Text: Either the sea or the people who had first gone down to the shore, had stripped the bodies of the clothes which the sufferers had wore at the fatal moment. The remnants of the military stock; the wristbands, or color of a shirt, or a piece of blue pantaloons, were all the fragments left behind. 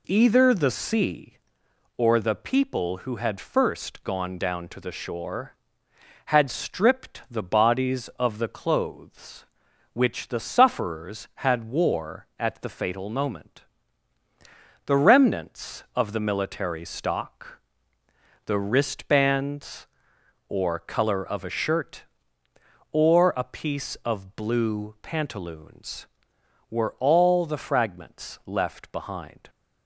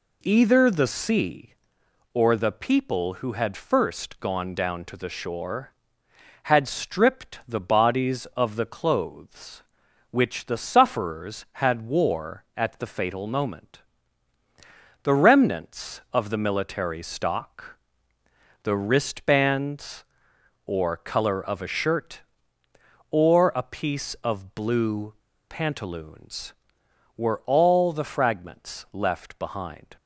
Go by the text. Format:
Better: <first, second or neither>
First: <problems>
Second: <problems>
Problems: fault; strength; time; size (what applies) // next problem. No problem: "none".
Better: first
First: none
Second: pauses between "blue" and "pantaloons"; slight; at 25.1 s; 0.34 s long